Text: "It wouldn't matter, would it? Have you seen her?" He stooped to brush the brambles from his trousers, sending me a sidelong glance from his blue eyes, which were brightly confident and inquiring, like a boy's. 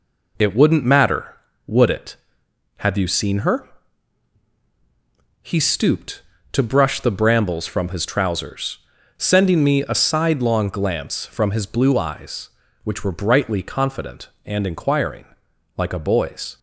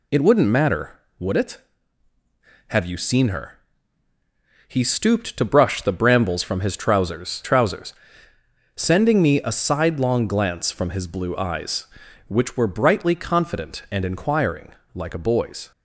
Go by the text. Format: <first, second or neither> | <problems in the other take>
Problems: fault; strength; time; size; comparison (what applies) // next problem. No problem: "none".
first | says "trousers" twice; at 7.4 s